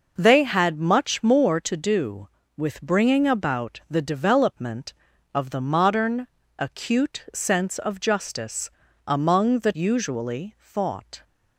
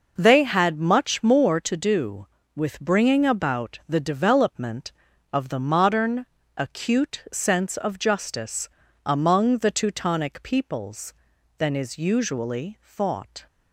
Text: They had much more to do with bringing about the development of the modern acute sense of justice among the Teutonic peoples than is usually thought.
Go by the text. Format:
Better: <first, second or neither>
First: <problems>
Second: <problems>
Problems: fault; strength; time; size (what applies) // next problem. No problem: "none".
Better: second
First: pauses between "modern" and "acute"; slight; at 6.2 s; 0.30 s long // pauses between "justice" and "among"; slight; at 8.6 s; 0.36 s long // skips "Teutonic peoples than is"; at 9.7 s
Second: pauses between "modern" and "acute"; slight; at 6.2 s; 0.30 s long // pauses between "justice" and "among"; slight; at 8.6 s; 0.36 s long